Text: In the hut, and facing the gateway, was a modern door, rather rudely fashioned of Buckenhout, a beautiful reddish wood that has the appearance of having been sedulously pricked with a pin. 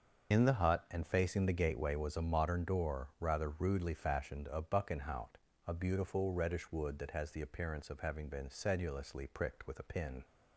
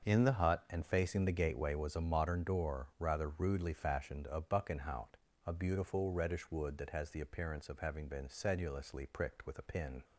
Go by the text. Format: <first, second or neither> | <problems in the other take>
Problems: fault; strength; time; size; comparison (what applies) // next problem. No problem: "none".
second | loses the start of "In"; at 0.3 s; 75 ms // starts louder than the rest; until 1.3 s; 6.5 dB; also in the second